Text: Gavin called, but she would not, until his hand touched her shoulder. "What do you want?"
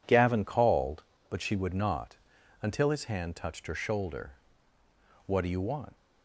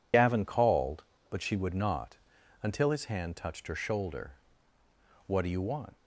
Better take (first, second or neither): first